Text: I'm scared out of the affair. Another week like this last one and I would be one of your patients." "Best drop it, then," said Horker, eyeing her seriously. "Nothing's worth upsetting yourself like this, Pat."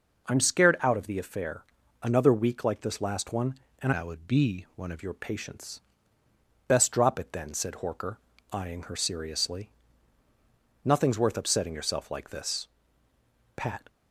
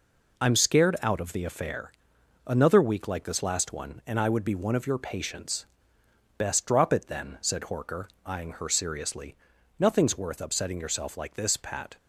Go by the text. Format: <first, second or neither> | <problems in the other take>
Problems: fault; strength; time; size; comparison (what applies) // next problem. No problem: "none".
second | changes voice from "I" to "of"; from 3.9 to 4.9 s; 1.0 s long